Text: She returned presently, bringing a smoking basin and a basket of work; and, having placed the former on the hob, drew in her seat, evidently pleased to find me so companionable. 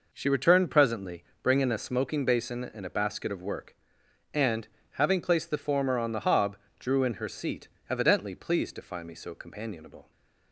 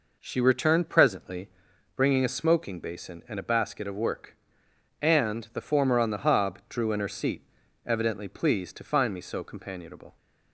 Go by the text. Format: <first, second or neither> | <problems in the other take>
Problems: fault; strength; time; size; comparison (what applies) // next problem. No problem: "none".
first | skips "having placed"; at 5.4 s